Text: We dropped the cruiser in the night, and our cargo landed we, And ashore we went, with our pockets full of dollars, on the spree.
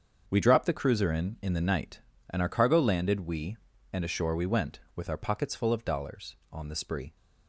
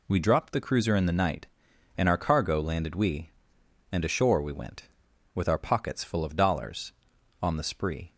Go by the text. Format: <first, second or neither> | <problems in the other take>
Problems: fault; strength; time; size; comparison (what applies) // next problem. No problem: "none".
second | starts louder than the rest; until 1.2 s; 7 dB // says "in" twice; at 1.3 s